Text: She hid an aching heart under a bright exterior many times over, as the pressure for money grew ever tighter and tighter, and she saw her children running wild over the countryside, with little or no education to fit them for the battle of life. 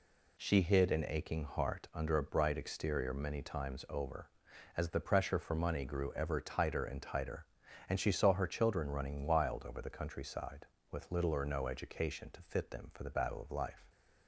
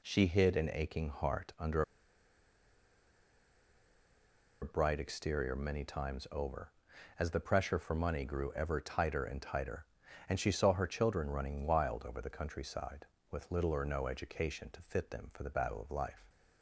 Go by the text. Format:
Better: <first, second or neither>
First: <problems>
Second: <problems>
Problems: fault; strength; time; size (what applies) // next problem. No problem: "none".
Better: first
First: none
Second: pauses between "under" and "a"; strong; at 1.8 s; 2.7 s long